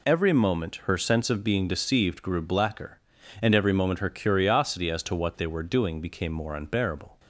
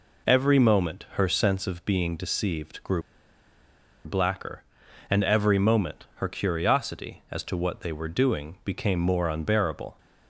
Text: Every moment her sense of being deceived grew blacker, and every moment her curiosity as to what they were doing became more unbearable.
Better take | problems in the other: first | pauses between "grew" and "blacker"; at 3.0 s; 1.0 s long

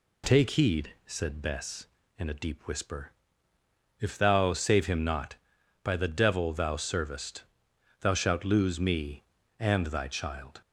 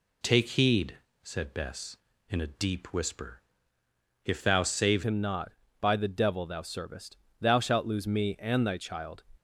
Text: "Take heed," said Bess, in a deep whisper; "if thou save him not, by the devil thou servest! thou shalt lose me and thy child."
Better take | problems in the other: first | changes voice at "him"; from 5.0 s on; 4.2 s long

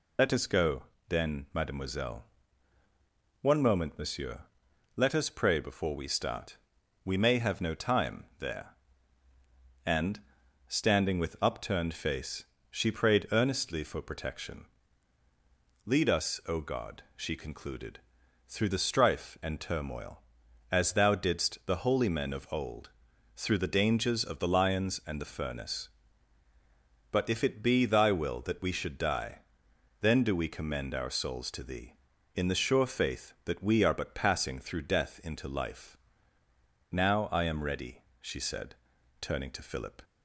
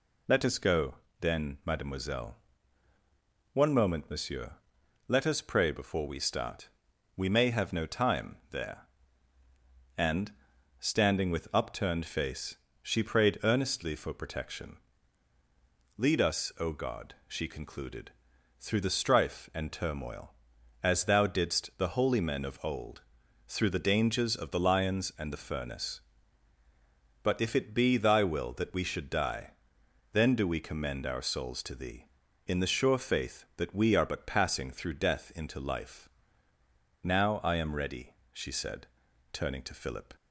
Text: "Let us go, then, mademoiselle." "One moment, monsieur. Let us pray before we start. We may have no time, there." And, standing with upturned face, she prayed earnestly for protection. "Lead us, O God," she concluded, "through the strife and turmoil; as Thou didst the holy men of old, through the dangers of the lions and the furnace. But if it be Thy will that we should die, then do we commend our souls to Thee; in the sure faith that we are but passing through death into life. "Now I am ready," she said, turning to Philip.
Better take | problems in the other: second | loses the start of "Let"; at 0.1 s; 35 ms

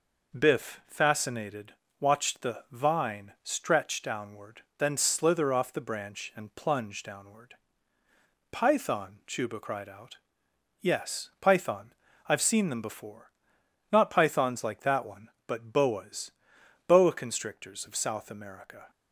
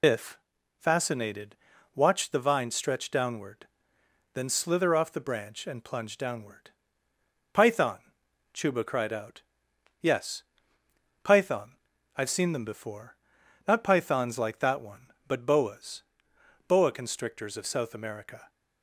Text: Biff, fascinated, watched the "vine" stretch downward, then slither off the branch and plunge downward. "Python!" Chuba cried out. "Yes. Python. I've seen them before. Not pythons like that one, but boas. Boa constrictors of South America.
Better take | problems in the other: first | loses the start of "Biff"; at 0.0 s; 80 ms

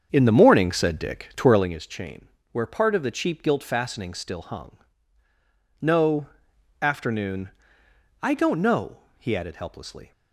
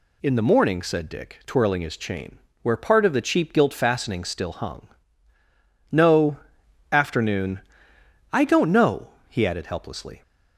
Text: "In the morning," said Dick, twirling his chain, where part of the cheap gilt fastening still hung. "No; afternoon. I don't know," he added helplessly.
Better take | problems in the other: second | starts louder than the rest; strong; until 1.8 s; 7 dB

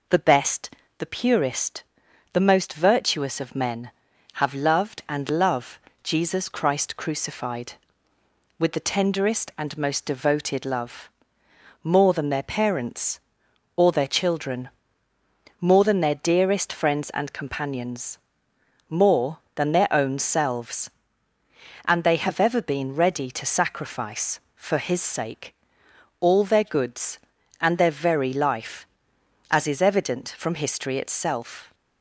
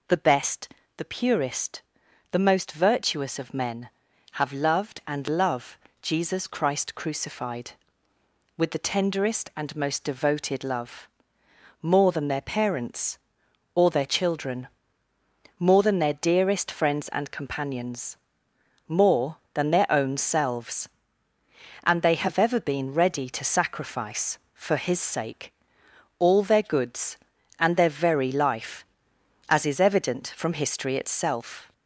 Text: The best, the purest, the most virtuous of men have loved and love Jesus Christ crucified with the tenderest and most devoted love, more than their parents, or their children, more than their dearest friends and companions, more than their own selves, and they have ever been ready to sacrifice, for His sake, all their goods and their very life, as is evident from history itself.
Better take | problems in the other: first | gets louder; slight; throughout; 2.5 dB // pauses between "love" and "Jesus"; slight; at 5.7 s; 0.24 s long; slight in the first

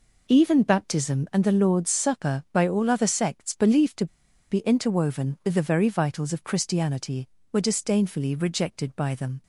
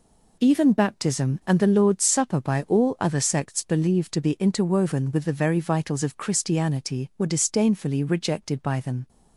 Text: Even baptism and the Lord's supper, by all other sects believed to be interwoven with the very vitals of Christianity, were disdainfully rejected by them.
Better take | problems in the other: second | pauses between "to" and "be"; at 4.0 s; 0.44 s long

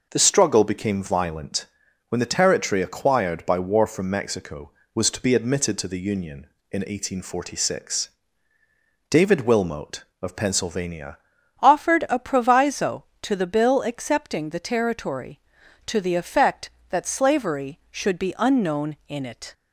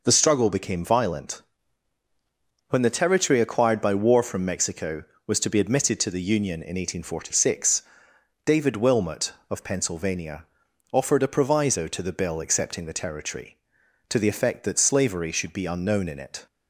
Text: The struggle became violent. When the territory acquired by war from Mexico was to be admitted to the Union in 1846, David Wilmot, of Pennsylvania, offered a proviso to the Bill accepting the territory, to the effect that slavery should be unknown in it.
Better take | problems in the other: second | changes voice at "offered"; from 11.6 s on; 7.9 s long

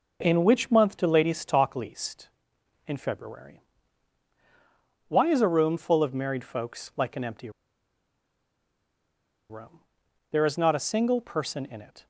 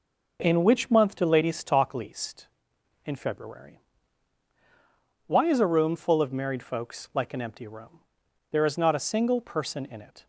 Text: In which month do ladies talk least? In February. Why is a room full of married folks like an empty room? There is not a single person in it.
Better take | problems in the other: second | pauses between "empty" and "room"; strong; at 7.4 s; 2.0 s long

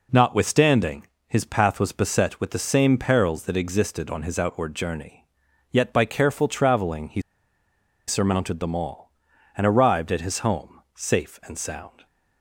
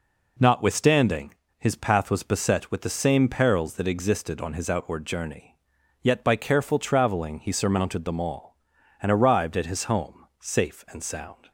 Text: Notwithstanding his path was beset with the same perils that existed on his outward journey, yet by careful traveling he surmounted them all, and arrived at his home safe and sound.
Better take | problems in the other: second | pauses between "Notwithstanding" and "his"; slight; at 1.0 s; 0.22 s long; slight in the second // pauses between "he" and "surmounted"; noticeable; at 7.1 s; 0.87 s long

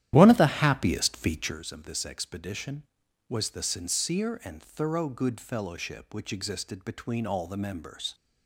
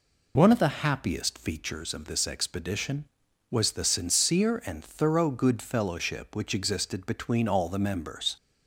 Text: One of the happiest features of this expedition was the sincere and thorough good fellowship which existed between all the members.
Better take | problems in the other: second | starts louder than the rest; strong; until 1.6 s; 11.5 dB

